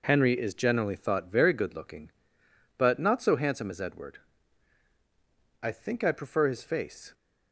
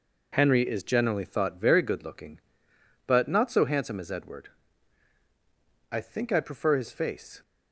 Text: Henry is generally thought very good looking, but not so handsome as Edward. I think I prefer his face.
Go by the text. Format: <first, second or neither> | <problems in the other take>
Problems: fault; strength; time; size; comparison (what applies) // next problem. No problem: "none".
neither | none